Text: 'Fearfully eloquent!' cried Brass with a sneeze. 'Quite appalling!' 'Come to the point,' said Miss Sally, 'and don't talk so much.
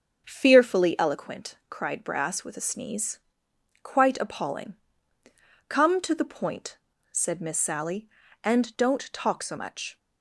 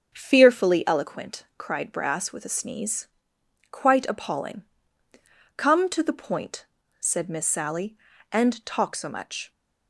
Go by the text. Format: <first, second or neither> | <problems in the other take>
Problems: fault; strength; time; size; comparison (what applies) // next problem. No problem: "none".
first | starts louder than the rest; strong; until 1.1 s; 7.5 dB; also in the first // skips "don't"; at 8.6 s